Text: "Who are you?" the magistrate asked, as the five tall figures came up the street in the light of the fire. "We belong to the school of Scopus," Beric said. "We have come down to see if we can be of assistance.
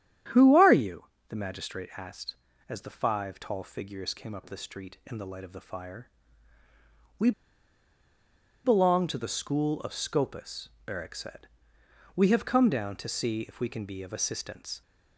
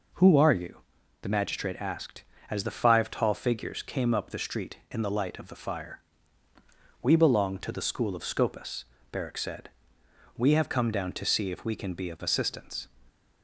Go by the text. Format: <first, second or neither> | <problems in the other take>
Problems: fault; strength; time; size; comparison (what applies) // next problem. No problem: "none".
second | starts louder than the rest; strong; until 1.5 s; 10 dB // pauses between "We" and "belong"; strong; at 7.3 s; 1.3 s long